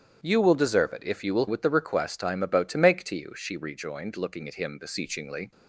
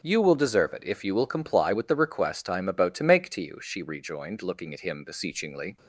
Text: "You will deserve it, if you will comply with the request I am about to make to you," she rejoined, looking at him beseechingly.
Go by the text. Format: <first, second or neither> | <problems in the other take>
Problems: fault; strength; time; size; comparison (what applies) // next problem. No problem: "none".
second | starts louder than the rest; strong; until 1.2 s; 10 dB // skips "comply"; at 1.4 s